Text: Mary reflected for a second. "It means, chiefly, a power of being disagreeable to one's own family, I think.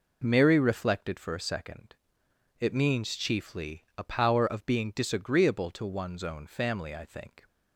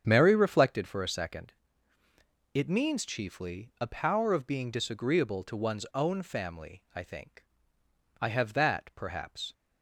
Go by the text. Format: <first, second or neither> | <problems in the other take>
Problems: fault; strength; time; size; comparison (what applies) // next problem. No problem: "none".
first | starts louder than the rest; strong; until 1.0 s; 7.5 dB // goes on to say "I have that perhaps"; from 8.1 s on; 1.3 s long